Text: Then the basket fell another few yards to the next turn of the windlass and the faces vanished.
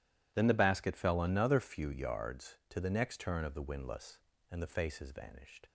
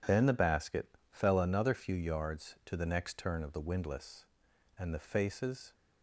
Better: first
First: none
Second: stops before "vanished"; at 5.7 s

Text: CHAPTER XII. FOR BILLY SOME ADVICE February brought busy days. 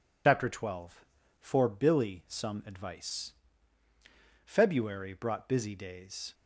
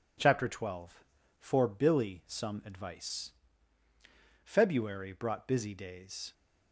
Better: second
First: loses the start of "CHAPTER"; at 0.2 s; 65 ms // pauses between "ADVICE" and "February"; at 3.3 s; 1.1 s long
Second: pauses between "ADVICE" and "February"; at 3.3 s; 1.1 s long

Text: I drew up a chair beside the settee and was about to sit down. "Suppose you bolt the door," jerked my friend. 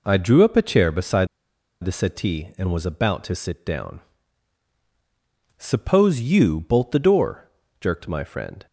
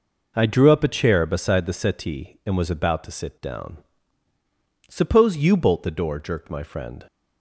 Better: second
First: pauses between "beside" and "the"; noticeable; at 1.2 s; 0.57 s long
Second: none

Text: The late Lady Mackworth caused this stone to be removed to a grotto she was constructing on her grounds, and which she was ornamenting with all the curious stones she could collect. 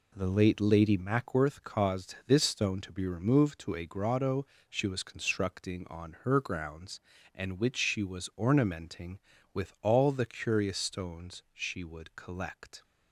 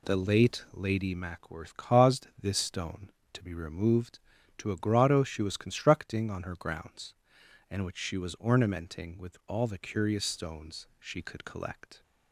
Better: second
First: pauses between "grotto" and "she"; slight; at 4.4 s; 0.24 s long // says "would" for "could"; at 11.8 s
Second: none

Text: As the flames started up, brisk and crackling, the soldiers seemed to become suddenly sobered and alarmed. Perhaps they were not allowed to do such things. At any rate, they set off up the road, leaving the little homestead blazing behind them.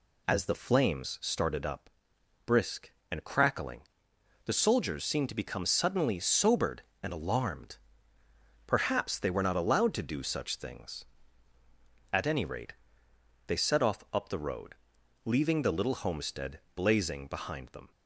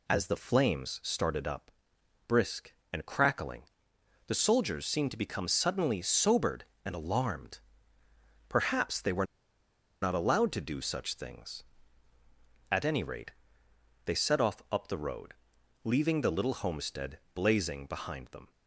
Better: first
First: none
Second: pauses between "were" and "not"; noticeable; at 9.2 s; 0.77 s long

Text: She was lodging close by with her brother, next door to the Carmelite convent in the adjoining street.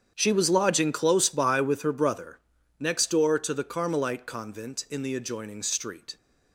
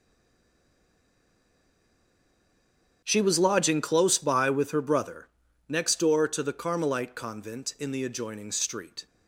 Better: first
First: starts louder than the rest; strong; until 1.1 s; 8.5 dB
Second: stays silent before the first word; strong; until 3.0 s; 3.0 s long // starts louder than the rest; strong; until 4.0 s; 8.5 dB

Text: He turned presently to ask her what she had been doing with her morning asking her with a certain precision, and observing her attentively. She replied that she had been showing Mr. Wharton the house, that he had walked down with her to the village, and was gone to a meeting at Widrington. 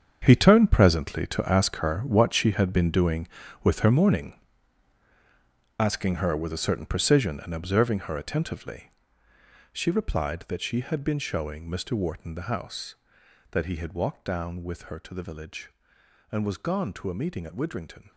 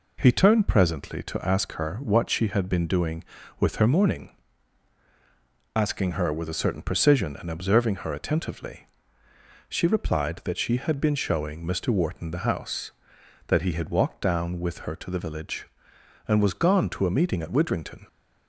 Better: second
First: gets quieter; strong; throughout; 12.5 dB // pauses between "morning" and "asking"; strong; at 4.3 s; 1.4 s long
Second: pauses between "morning" and "asking"; strong; at 4.3 s; 1.4 s long

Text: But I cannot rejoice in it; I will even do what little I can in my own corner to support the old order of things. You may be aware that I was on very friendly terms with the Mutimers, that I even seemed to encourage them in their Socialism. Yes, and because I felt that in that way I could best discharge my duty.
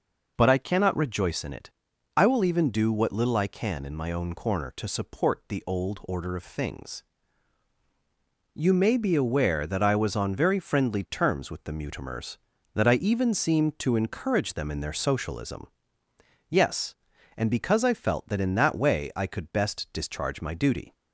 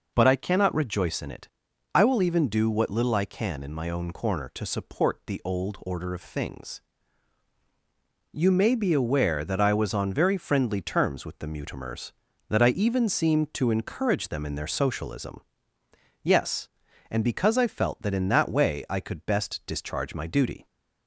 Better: neither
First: none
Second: none

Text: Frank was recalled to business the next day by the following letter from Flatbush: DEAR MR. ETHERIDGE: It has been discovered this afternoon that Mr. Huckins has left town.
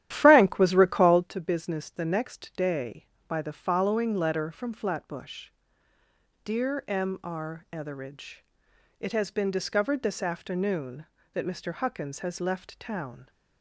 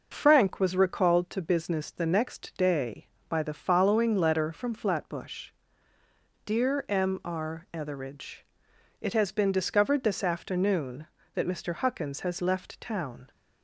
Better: second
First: starts louder than the rest; strong; until 1.3 s; 12 dB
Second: none

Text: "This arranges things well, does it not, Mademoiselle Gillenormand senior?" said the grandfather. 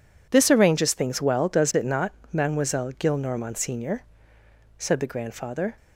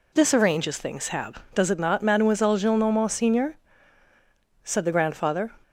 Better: first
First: none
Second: says "hab" for "well"; at 1.0 s

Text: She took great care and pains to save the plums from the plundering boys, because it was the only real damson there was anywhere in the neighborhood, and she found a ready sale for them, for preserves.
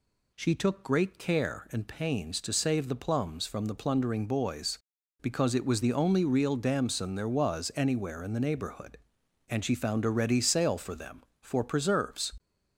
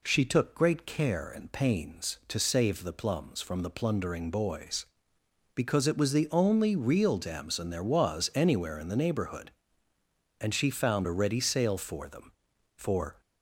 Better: first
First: none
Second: stops before "preserves"; at 13.2 s

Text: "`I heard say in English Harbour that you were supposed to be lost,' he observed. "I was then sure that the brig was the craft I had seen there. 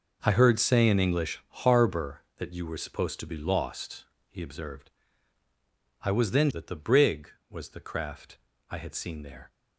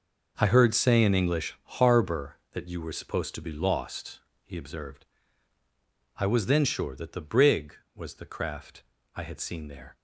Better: second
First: pauses between "English" and "Harbour"; slight; at 1.3 s; 0.24 s long // skips "sure"; at 6.4 s // pauses between "craft" and "I"; slight; at 8.3 s; 0.34 s long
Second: pauses between "English" and "Harbour"; slight; at 1.5 s; 0.24 s long // pauses between "craft" and "I"; slight; at 8.8 s; 0.34 s long

